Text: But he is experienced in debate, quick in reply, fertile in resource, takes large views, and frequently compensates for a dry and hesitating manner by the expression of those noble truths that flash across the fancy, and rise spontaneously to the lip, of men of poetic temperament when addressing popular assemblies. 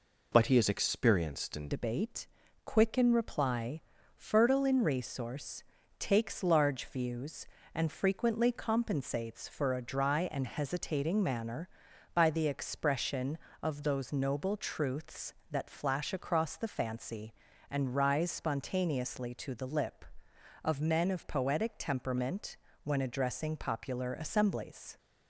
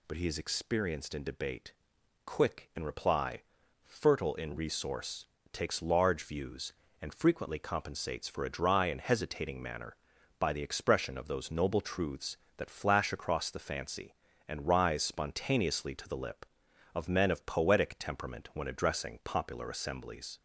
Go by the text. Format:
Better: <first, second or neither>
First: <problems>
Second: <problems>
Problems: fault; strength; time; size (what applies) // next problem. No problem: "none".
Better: second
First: changes voice at "debate"; from 1.7 s on; 23.2 s long // pauses between "temperament" and "when"; slight; at 22.5 s; 0.26 s long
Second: none